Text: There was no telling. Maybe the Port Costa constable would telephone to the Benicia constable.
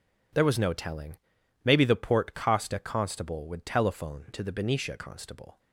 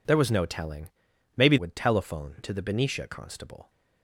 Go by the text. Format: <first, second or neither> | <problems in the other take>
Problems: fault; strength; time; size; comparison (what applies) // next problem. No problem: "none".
first | skips "the Port Costa constable"; at 1.5 s